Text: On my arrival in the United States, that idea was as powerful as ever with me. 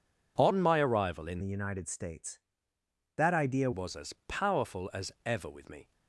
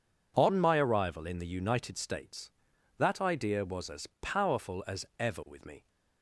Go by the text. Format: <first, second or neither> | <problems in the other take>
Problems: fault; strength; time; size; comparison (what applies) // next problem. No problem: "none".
second | changes voice from "the" to "idea"; from 1.3 to 3.6 s; 2.3 s long // pauses between "as" and "powerful"; slight; at 4.1 s; 0.16 s long; slight in the second